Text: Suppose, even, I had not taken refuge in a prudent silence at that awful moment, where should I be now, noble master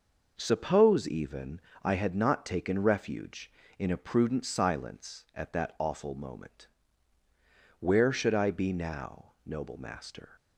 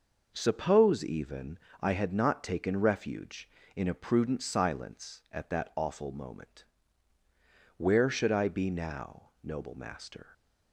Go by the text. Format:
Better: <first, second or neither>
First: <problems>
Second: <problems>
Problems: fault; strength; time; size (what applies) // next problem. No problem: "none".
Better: neither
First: none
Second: none